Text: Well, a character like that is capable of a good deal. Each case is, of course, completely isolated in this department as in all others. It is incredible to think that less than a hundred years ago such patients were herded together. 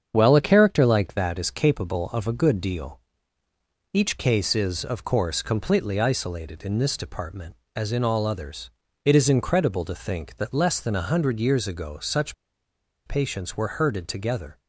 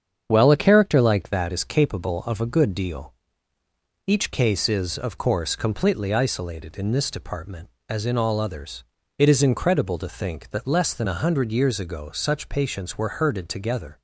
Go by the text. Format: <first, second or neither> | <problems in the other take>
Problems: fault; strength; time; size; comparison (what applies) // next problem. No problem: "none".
second | starts louder than the rest; strong; until 1.1 s; 7.5 dB; strong in the second // pauses between "such" and "patients"; noticeable; at 12.3 s; 0.71 s long